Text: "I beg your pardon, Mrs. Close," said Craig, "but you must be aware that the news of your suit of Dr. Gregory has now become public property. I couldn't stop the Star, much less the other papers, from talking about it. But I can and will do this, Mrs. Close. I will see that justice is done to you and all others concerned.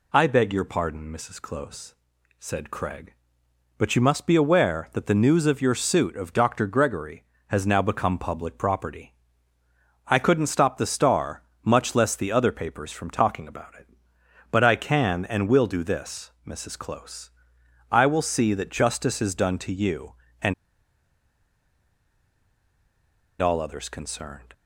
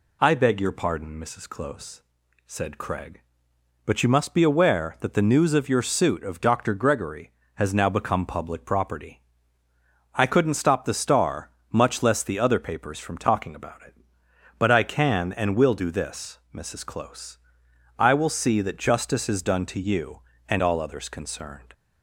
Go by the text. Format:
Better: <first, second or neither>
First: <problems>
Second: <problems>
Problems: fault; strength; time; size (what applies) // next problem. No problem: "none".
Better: second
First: pauses between "and" and "all"; strong; at 20.5 s; 2.8 s long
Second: none